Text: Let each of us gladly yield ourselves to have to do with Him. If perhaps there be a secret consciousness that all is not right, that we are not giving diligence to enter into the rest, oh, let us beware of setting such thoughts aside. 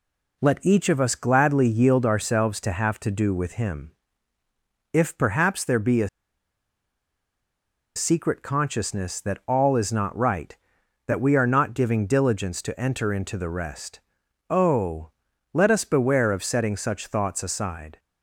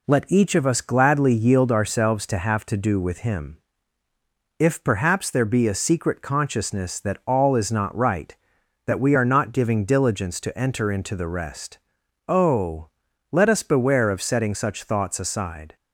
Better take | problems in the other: second | pauses between "a" and "secret"; strong; at 6.0 s; 1.8 s long

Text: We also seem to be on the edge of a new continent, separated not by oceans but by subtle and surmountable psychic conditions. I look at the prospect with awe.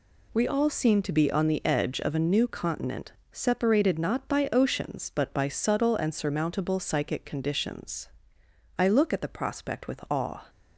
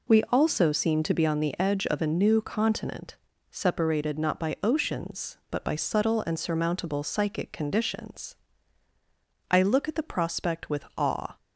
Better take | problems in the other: second | says "all" for "also"; at 0.4 s

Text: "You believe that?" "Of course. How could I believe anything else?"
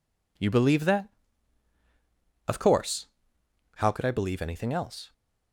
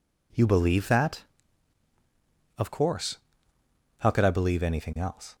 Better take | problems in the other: neither | none

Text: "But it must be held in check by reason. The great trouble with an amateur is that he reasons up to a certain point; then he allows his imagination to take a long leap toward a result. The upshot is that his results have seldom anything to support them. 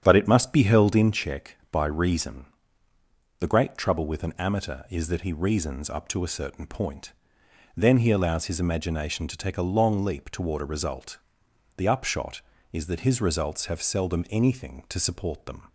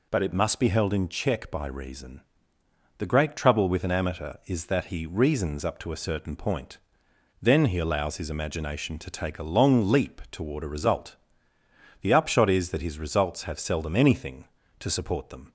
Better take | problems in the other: second | starts louder than the rest; strong; until 1.2 s; 8.5 dB

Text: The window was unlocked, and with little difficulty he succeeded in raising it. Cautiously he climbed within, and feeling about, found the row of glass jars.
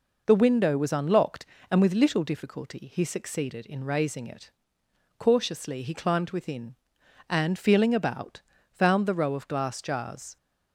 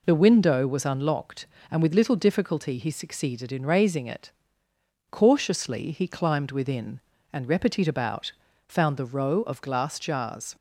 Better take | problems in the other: first | says "repetit" for "feeling"; at 7.4 s

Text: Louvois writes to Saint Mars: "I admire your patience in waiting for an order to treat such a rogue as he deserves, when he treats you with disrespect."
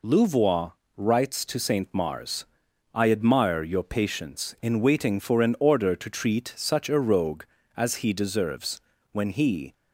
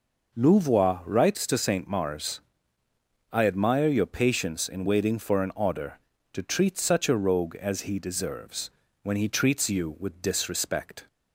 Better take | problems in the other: second | pauses between "Louvois" and "writes"; slight; at 0.7 s; 0.26 s long // stops before "treats you with disrespect"; at 9.7 s

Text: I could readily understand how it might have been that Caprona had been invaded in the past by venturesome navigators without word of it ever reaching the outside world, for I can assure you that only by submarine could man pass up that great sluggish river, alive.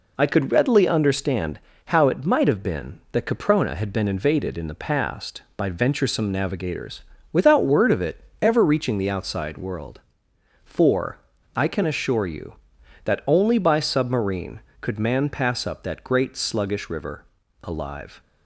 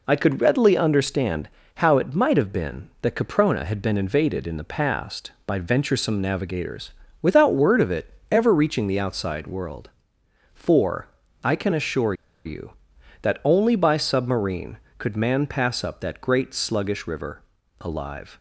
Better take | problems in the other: first | pauses between "understand" and "how"; slight; at 1.4 s; 0.26 s long; slight in the first // pauses between "navigators" and "without"; slight; at 6.9 s; 0.30 s long; slight in the first // pauses between "it" and "ever"; slight; at 8.1 s; 0.18 s long; slight in the first // pauses between "for" and "I"; at 11.0 s; 0.38 s long; also in the first // pauses between "assure" and "you"; slight; at 12.1 s; 0.30 s long

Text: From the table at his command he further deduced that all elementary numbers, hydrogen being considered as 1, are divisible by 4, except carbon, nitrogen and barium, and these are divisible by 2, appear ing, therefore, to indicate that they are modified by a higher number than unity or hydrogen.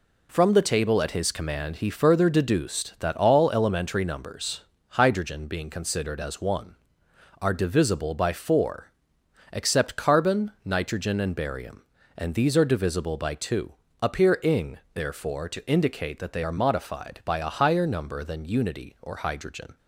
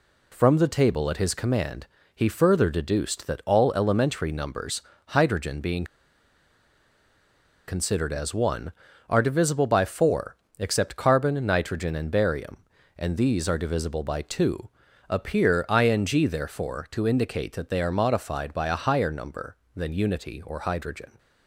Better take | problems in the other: first | pauses between "command" and "he"; slight; at 1.8 s; 0.30 s long // pauses between "being" and "considered"; strong; at 5.8 s; 1.8 s long

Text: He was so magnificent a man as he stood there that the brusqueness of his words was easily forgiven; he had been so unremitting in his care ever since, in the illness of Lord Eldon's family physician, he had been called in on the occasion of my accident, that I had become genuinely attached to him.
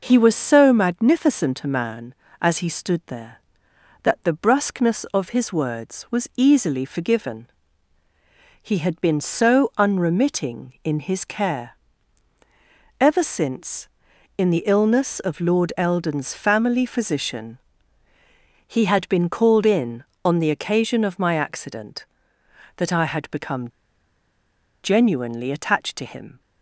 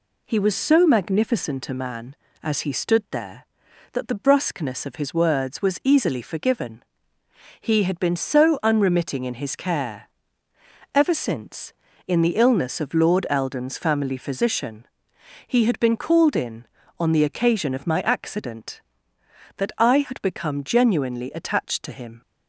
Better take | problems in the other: second | pauses between "care" and "ever"; at 11.7 s; 1.2 s long; noticeable in the second // pauses between "become" and "genuinely"; at 23.6 s; 1.1 s long

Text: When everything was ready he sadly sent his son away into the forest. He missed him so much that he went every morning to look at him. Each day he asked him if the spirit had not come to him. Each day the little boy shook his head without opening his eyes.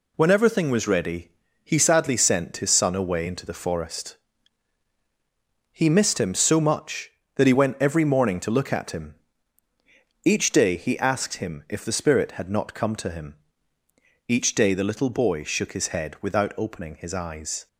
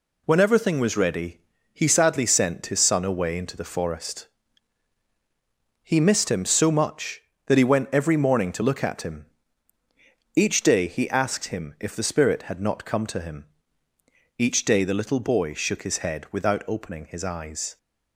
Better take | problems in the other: neither | pauses between "ready" and "he"; slight; the same in both

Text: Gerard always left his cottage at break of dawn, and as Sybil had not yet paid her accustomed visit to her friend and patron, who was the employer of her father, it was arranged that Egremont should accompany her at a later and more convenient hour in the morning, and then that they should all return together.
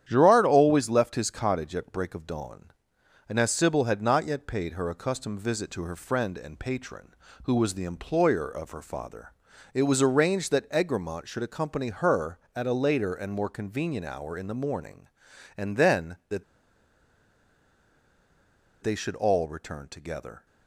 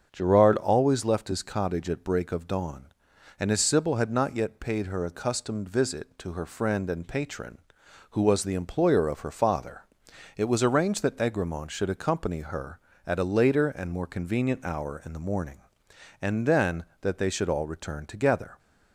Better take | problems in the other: second | starts louder than the rest; strong; until 1.0 s; 10 dB; strong in the second // pauses between "that" and "they"; strong; at 16.4 s; 2.3 s long

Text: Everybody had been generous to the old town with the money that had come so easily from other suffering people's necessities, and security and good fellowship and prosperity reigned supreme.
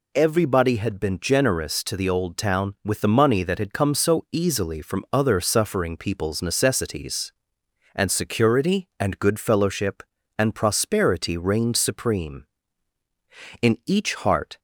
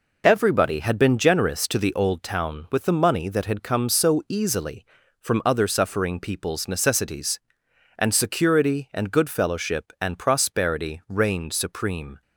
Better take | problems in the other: second | goes on to say "In each heart"; noticeable; from 13.6 s on; 0.98 s long

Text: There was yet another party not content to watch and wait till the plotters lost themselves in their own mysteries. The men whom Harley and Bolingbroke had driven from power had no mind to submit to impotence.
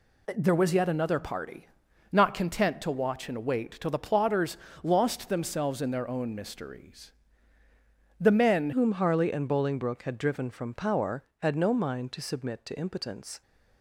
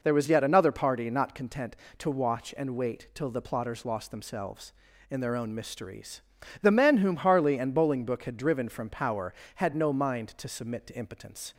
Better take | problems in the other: second | pauses between "party" and "not"; at 1.6 s; 0.44 s long // pauses between "plotters" and "lost"; slight; at 4.5 s; 0.28 s long // changes voice at "whom"; from 8.7 s on; 4.7 s long

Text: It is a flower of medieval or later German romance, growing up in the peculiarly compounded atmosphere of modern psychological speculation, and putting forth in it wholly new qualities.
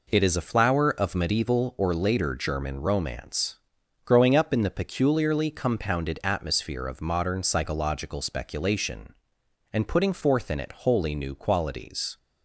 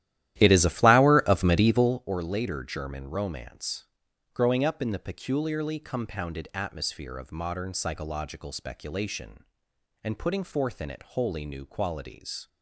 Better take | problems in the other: first | starts louder than the rest; strong; until 2.1 s; 13.5 dB

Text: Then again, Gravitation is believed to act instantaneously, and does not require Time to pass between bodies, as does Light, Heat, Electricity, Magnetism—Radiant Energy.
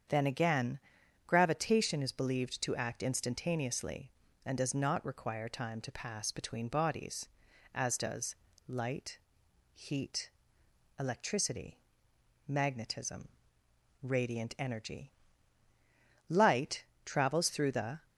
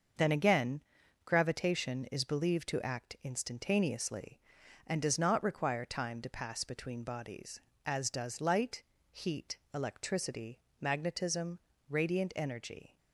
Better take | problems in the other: second | starts louder than the rest; strong; until 1.5 s; 7.5 dB; also in the second // pauses between "does" and "Light"; slight; at 8.3 s; 0.32 s long // goes on to say "Light travels through the"; from 16.4 s on; 1.6 s long

